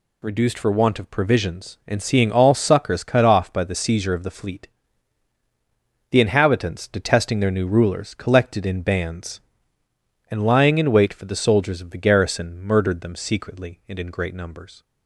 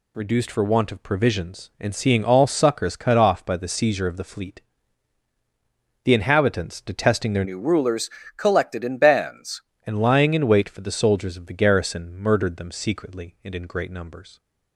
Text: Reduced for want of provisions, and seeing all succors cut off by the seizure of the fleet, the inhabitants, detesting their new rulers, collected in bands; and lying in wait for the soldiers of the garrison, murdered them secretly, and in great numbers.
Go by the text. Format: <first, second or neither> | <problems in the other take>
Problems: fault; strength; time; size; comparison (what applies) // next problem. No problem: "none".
first | changes voice from "new" to "bands"; from 7.4 to 9.6 s; 2.2 s long